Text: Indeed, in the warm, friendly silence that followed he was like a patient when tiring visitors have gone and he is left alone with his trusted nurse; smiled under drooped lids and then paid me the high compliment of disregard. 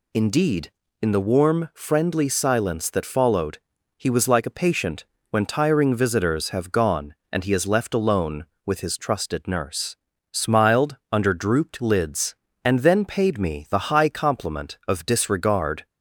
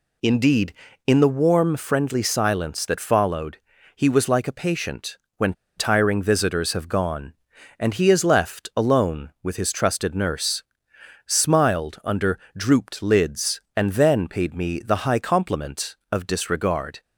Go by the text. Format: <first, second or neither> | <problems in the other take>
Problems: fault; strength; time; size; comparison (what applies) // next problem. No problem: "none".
first | pauses between "followed" and "he"; at 3.5 s; 0.38 s long; also in the first // pauses between "patient" and "when"; slight; at 5.1 s; 0.18 s long; slight in the first // pauses between "when" and "tiring"; slight; at 5.5 s; 0.24 s long // pauses between "under" and "drooped"; slight; at 12.3 s; 0.16 s long